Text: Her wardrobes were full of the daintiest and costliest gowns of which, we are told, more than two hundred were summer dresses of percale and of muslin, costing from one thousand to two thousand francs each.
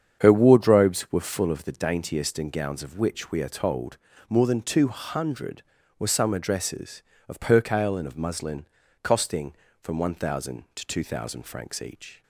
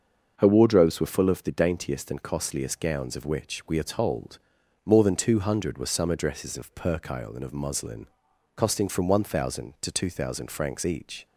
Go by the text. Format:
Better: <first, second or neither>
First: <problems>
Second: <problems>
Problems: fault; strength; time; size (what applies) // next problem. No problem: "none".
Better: second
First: starts louder than the rest; strong; until 1.2 s; 8 dB // skips "costliest"; at 2.4 s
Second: starts louder than the rest; until 1.3 s; 6.5 dB